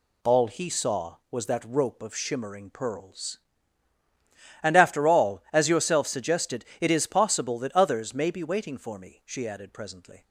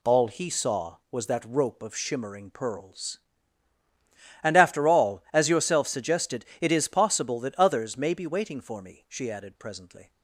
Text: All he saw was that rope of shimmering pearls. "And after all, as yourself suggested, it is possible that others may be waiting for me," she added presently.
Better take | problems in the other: neither | none

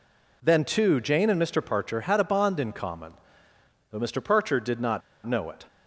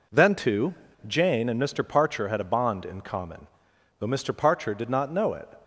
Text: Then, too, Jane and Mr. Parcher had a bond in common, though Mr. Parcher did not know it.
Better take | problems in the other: second | pauses between "not" and "know"; slight; at 5.0 s; 0.25 s long

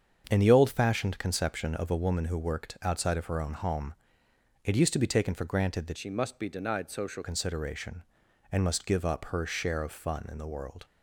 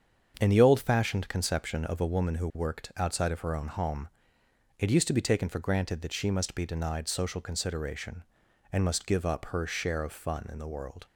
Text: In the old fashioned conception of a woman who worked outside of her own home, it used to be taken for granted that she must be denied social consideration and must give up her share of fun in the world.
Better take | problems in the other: second | starts louder than the rest; strong; until 1.3 s; 7.5 dB; strong in the second // changes voice from "she" to "social"; from 5.9 to 7.2 s; 1.3 s long

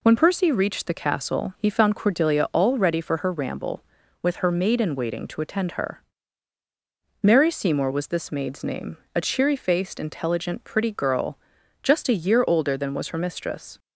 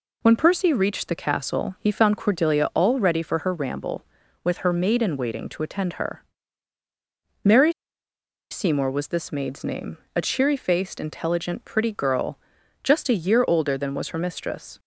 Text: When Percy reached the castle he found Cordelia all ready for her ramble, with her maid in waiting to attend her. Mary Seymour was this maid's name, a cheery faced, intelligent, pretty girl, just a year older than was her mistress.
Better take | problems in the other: first | pauses between "Mary" and "Seymour"; noticeable; at 7.7 s; 0.79 s long

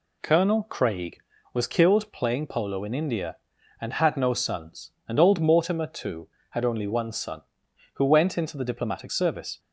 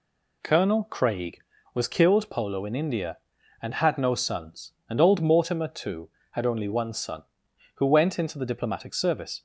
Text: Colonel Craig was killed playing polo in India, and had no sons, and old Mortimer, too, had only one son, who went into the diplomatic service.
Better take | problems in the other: first | skips "playing"; at 2.3 s

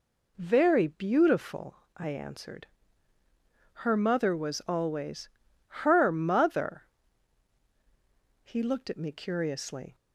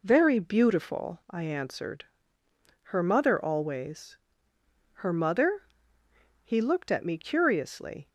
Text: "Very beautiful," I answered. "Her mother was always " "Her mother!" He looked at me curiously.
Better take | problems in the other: first | skips "was"; at 3.4 s

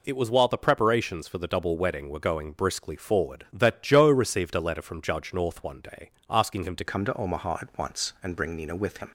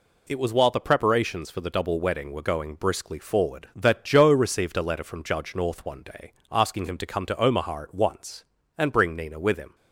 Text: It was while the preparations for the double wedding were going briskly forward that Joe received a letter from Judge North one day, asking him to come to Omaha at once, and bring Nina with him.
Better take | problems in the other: second | changes voice at "come"; from 6.8 s on; 2.3 s long

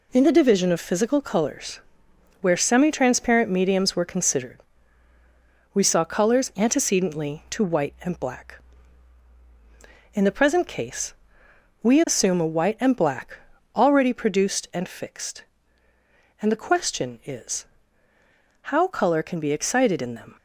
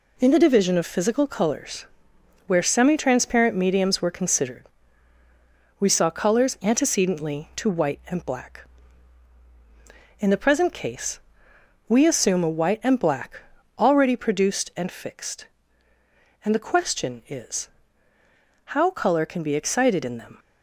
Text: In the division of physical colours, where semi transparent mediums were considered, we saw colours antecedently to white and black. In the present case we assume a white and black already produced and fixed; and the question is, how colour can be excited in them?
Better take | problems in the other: neither | pauses between "case" and "we"; noticeable; the same in both // pauses between "black" and "already"; slight; the same in both

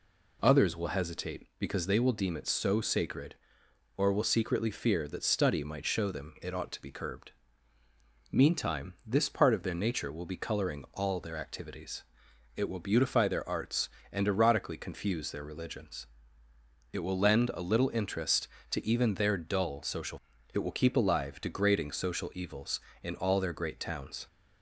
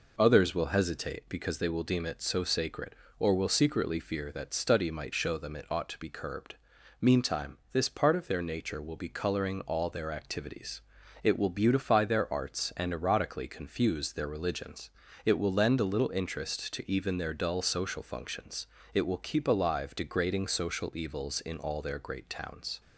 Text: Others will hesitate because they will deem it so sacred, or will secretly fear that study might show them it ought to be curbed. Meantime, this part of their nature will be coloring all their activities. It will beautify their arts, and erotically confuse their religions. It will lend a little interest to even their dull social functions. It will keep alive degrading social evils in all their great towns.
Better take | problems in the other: second | skips "functions"; at 20.3 s

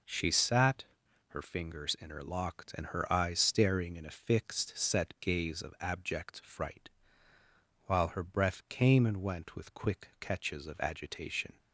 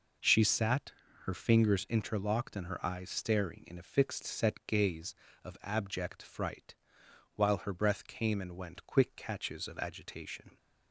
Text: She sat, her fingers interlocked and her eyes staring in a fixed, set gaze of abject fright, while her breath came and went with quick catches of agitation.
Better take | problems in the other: first | skips "with"; at 8.8 s

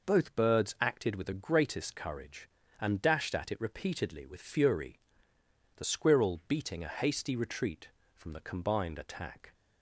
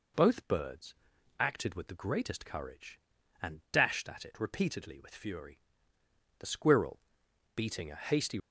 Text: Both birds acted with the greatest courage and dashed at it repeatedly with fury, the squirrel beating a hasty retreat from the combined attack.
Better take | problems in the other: first | pauses between "birds" and "acted"; at 0.9 s; 0.44 s long // pauses between "squirrel" and "beating"; noticeable; at 6.9 s; 0.54 s long // stops before "retreat from the combined attack"; at 8.3 s

